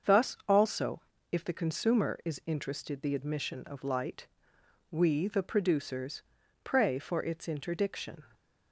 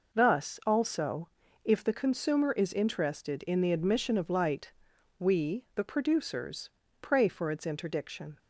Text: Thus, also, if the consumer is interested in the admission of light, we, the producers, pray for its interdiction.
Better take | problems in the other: second | starts louder than the rest; until 1.4 s; 7 dB // skips "in"; at 3.0 s

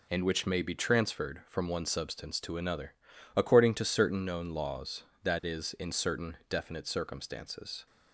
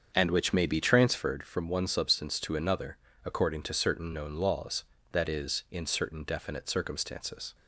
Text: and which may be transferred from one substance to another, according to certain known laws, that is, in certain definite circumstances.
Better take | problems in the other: first | starts louder than the rest; until 1.3 s; 7 dB

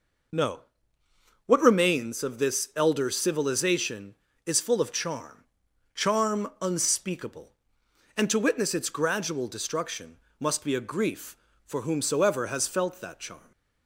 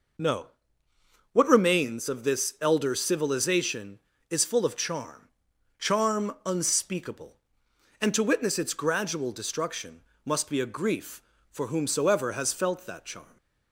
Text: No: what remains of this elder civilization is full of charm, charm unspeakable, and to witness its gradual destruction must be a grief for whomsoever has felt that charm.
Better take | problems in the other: neither | pauses between "destruction" and "must"; slight; the same in both

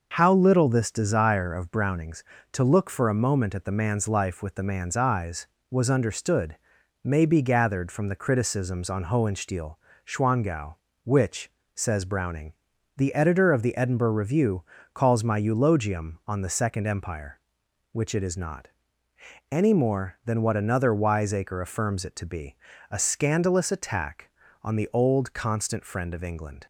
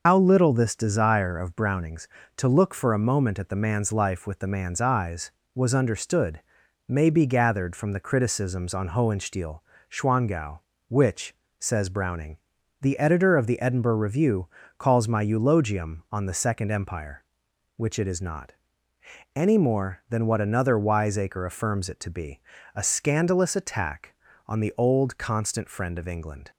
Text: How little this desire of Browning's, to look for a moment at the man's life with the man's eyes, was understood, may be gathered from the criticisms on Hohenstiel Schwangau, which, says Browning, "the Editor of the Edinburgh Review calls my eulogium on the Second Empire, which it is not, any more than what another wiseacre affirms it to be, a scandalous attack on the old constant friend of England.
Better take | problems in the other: first | loses the start of "How"; at 0.0 s; 100 ms // pauses between "Hohenstiel" and "Schwangau"; slight; at 9.6 s; 0.30 s long; slight in the first // pauses between "Review" and "calls"; slight; at 14.4 s; 0.28 s long; slight in the first

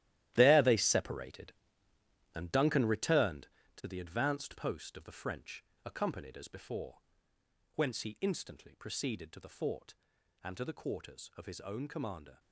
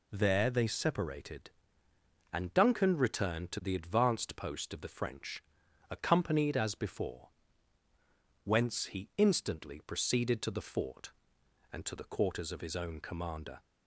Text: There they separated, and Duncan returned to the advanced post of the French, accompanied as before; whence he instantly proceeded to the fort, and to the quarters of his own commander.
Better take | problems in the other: second | gets quieter; strong; throughout; 12.5 dB

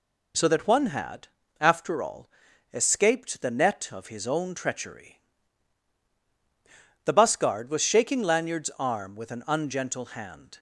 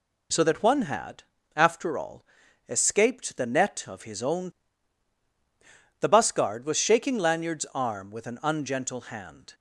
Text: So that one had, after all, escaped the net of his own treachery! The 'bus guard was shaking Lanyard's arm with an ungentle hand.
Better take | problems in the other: first | skips "treachery"; at 5.2 s

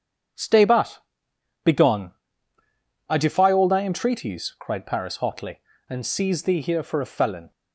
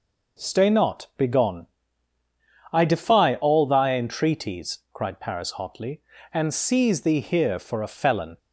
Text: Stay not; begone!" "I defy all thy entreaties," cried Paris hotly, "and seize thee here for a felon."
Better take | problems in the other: second | starts louder than the rest; strong; until 2.0 s; 8 dB // says "but" for "not"; at 0.6 s

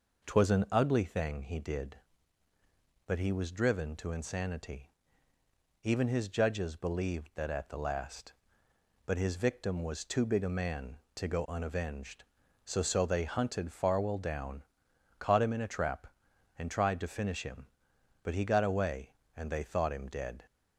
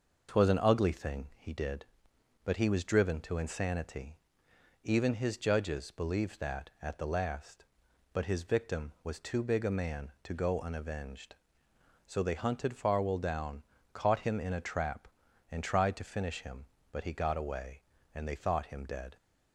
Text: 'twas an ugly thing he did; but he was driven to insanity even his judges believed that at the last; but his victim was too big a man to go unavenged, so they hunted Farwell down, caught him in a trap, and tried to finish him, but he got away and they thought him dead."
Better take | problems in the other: second | pauses between "insanity" and "even"; noticeable; at 4.8 s; 0.96 s long; noticeable in the second // says "so" twice; at 12.8 s

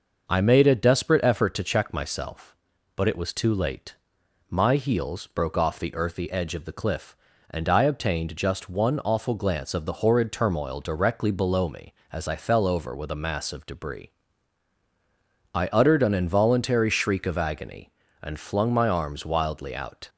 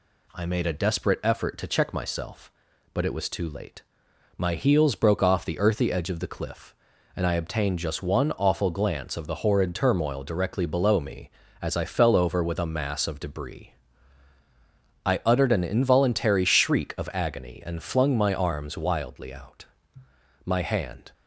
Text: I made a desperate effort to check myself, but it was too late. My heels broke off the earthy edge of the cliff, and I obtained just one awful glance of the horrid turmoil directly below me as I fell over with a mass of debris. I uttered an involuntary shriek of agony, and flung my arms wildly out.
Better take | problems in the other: first | goes on to say "My hand"; noticeable; from 20.4 s on; 0.66 s long

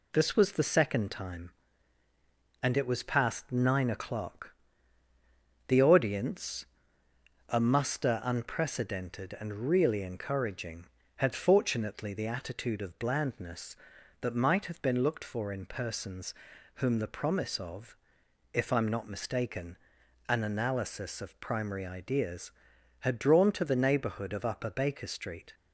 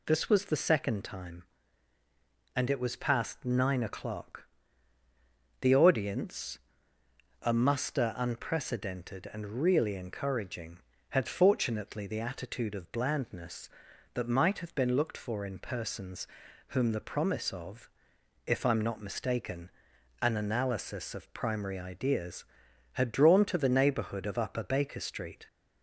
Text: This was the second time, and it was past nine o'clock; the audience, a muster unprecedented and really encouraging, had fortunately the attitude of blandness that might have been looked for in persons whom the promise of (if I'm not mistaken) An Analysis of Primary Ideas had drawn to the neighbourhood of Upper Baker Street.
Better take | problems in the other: second | gets quieter; slight; throughout; 3 dB // pauses between "persons" and "whom"; at 16.3 s; 0.42 s long; also in the second

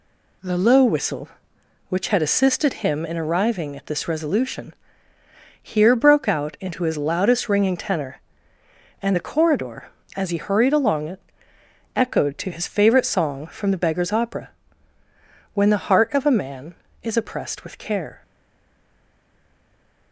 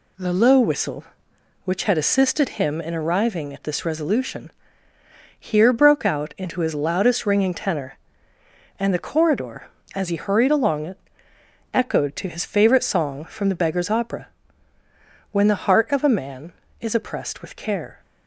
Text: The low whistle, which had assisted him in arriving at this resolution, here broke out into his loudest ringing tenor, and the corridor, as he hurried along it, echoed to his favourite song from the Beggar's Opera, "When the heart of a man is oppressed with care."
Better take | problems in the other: second | stays silent after the last word; noticeable; from 18.2 s on; 1.9 s long

